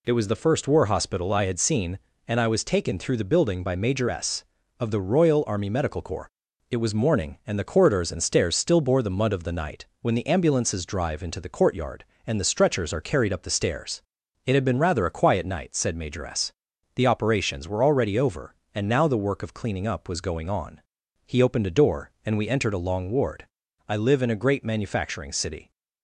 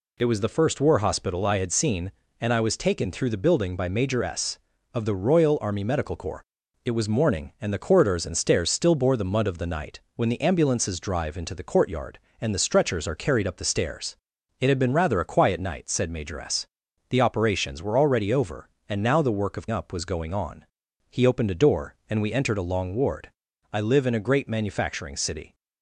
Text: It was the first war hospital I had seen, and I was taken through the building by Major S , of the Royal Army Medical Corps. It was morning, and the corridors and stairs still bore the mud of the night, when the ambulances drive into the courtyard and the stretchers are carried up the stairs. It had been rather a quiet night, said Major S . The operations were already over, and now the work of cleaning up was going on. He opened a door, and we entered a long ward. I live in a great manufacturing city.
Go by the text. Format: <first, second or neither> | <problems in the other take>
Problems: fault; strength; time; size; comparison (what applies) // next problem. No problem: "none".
first | skips "cleaning"; at 19.6 s